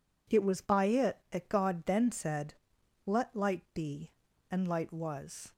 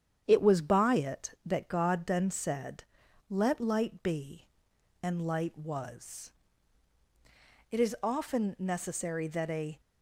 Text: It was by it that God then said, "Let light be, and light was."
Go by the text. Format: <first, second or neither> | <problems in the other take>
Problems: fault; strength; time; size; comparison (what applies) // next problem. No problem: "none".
first | starts louder than the rest; strong; until 1.2 s; 8.5 dB // goes on to say "It is often necessary that a"; strong; from 7.6 s on; 2.1 s long